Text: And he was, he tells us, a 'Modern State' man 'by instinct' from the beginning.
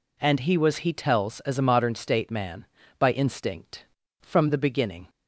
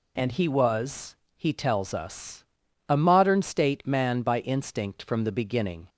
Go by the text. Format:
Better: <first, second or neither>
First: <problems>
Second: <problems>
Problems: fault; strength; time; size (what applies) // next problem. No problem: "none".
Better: second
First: says "as" for "us"; at 1.4 s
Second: none